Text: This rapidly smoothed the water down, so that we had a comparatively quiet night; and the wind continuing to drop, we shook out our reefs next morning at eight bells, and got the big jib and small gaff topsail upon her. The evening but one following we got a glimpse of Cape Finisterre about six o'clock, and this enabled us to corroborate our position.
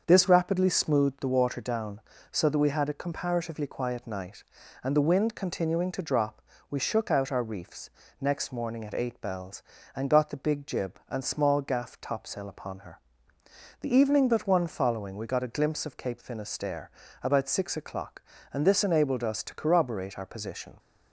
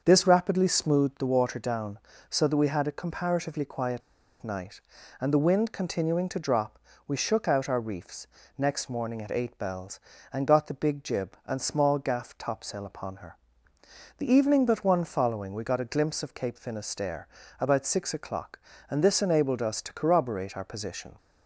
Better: first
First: starts louder than the rest; until 1.0 s; 6.5 dB // pauses between "reefs" and "next"; slight; at 7.8 s; 0.30 s long // pauses between "Finisterre" and "about"; slight; at 16.8 s; 0.32 s long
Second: starts louder than the rest; until 1.0 s; 6.5 dB // pauses between "quiet" and "night"; at 4.0 s; 0.41 s long // pauses between "reefs" and "next"; slight; at 8.2 s; 0.30 s long // pauses between "Finisterre" and "about"; slight; at 17.2 s; 0.32 s long

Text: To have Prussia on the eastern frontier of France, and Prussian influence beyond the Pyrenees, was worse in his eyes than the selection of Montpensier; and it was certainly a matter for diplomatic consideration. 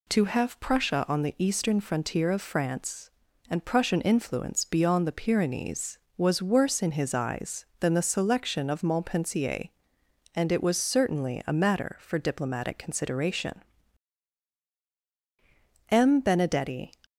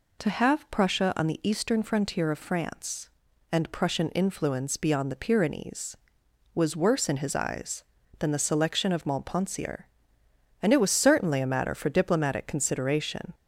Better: second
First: goes on to say "M Benedetti"; noticeable; from 15.9 s on; 1.0 s long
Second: none

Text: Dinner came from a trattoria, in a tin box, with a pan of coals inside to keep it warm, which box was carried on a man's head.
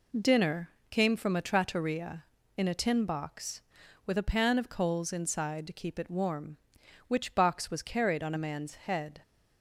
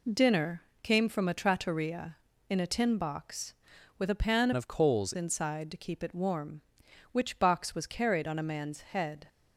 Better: first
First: pauses between "Dinner" and "came"; slight; at 0.6 s; 0.22 s long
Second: pauses between "Dinner" and "came"; slight; at 0.6 s; 0.22 s long // changes voice from "of" to "coals"; from 4.5 to 5.1 s; 0.6 s long

